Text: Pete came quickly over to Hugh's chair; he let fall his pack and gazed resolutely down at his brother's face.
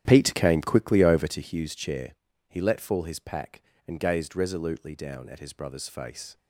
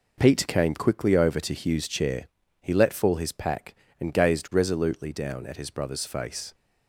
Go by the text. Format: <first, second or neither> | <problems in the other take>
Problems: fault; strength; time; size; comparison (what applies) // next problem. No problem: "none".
second | starts louder than the rest; strong; until 1.4 s; 11 dB